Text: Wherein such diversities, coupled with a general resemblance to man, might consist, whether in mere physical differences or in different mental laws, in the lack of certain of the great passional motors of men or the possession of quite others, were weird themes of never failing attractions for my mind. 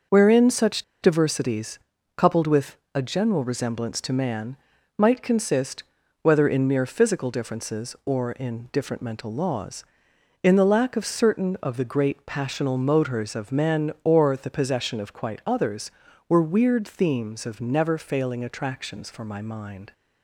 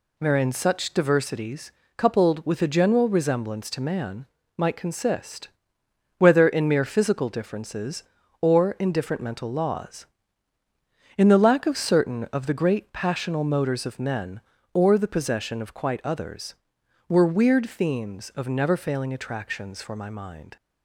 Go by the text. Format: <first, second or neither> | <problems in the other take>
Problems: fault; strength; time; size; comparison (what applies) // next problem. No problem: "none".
second | starts louder than the rest; until 1.3 s; 6 dB // pauses between "such" and "diversities"; slight; at 0.8 s; 0.19 s long // pauses between "with" and "a"; slight; at 2.7 s; 0.18 s long